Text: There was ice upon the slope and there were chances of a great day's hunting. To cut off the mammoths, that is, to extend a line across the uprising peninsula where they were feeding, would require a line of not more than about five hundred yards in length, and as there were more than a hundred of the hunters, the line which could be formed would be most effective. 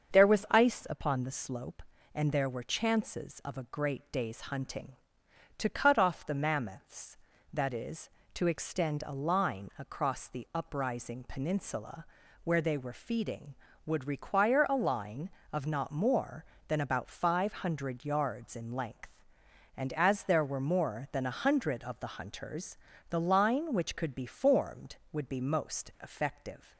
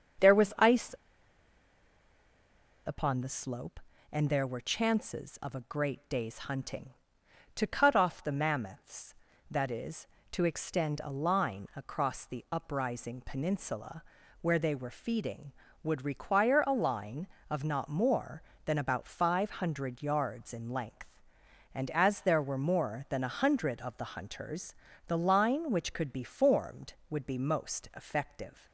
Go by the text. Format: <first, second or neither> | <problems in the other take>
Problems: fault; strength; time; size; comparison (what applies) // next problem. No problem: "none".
first | starts louder than the rest; until 3.2 s; 7 dB; also in the first // pauses between "ice" and "upon"; strong; at 0.9 s; 1.9 s long // pauses between "peninsula" and "where"; at 14.0 s; 0.40 s long; also in the first